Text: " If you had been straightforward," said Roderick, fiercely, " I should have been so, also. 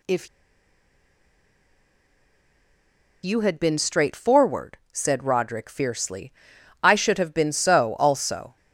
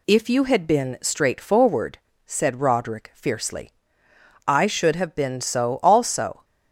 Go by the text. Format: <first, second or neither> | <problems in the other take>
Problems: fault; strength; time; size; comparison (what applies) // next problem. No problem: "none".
second | pauses between "If" and "you"; strong; at 0.2 s; 2.9 s long